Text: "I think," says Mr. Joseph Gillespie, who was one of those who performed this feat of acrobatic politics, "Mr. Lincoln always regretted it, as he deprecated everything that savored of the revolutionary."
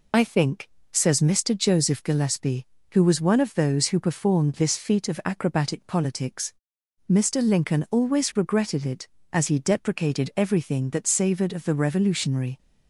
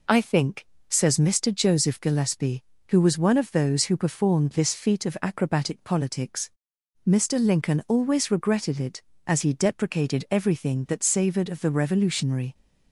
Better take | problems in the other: second | loses the start of "I"; at 0.1 s; 30 ms

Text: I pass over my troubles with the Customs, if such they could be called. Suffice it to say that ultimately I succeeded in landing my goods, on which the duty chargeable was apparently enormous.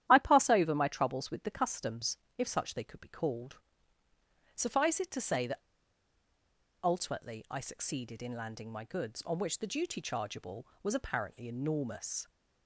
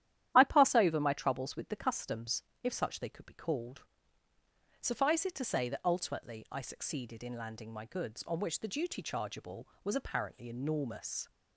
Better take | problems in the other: second | starts louder than the rest; strong; until 1.1 s; 11.5 dB; strong in the second // pauses between "that" and "ultimately"; strong; at 5.5 s; 1.2 s long

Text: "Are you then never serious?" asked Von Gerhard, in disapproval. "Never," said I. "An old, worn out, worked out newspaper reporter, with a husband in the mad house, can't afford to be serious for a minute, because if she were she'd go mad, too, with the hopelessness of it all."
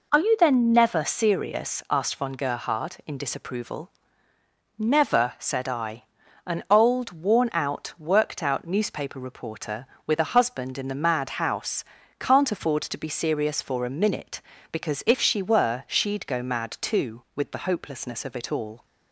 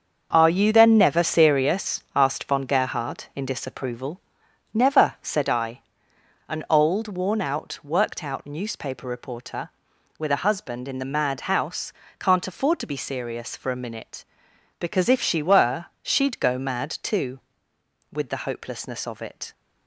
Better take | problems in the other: first | starts louder than the rest; until 1.3 s; 6.5 dB // stops before "all"; at 19.5 s

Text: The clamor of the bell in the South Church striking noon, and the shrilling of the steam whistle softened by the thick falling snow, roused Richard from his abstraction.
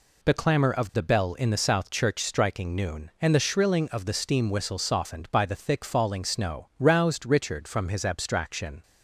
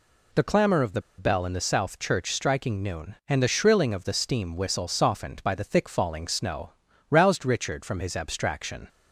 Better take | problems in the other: first | pauses between "the" and "bell"; slight; at 1.0 s; 0.16 s long

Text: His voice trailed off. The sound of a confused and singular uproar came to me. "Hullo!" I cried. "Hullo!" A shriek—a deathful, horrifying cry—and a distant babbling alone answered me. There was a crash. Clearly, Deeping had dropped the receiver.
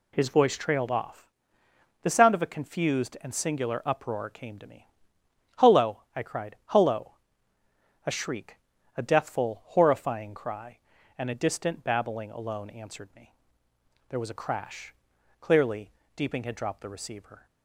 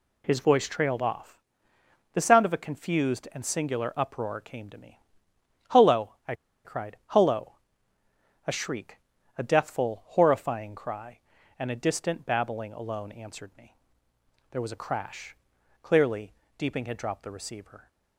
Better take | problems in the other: first | pauses between "I" and "cried"; slight; at 6.3 s; 0.31 s long

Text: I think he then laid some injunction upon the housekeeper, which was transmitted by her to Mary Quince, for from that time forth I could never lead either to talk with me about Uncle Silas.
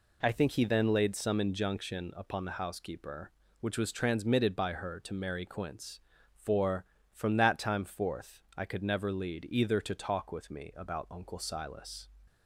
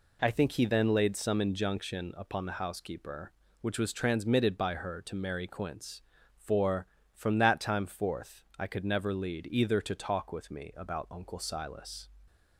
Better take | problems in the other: neither | none

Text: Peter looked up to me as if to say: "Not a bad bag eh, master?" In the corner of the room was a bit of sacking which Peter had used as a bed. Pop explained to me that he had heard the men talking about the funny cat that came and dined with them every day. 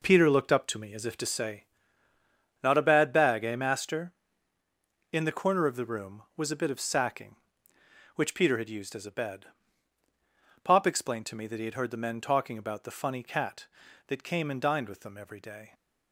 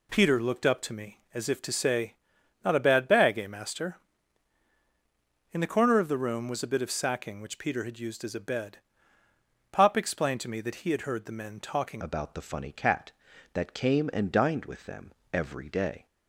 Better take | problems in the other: first | changes voice at "about"; from 12.0 s on; 4.0 s long // pauses between "them" and "every"; slight; at 15.1 s; 0.20 s long

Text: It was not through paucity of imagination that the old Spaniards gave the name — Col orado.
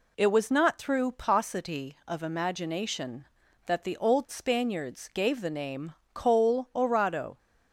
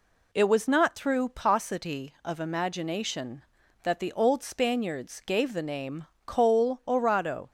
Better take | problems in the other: neither | none

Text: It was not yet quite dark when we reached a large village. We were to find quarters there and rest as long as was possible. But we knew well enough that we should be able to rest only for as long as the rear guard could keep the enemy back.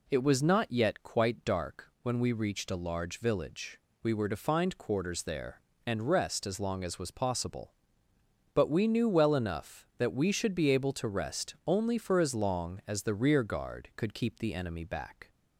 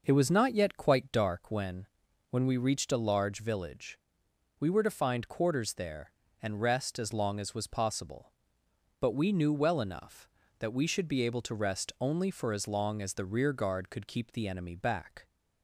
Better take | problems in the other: first | says "when" twice; at 2.2 s

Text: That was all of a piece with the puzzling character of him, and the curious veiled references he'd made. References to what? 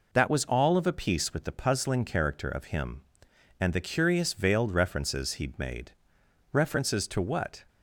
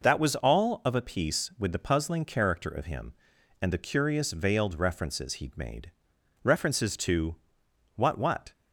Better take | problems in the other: first | pauses between "to" and "what"; noticeable; at 7.3 s; 0.58 s long // says "what" twice; at 8.1 s

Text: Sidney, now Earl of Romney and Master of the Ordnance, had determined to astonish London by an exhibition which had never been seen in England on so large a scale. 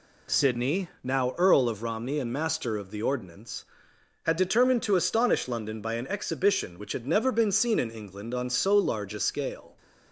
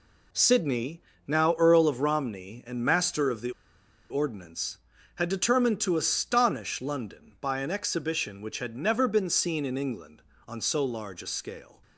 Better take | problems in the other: first | pauses between "the" and "Ordnance"; noticeable; at 3.5 s; 0.59 s long

